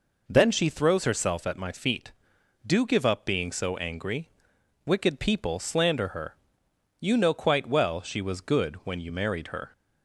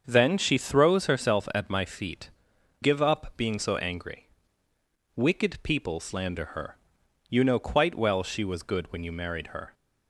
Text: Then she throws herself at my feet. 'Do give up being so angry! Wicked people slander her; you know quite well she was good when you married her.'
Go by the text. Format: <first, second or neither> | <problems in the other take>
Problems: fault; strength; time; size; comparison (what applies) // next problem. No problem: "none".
first | starts louder than the rest; until 1.0 s; 7 dB // skips "Do"; at 2.5 s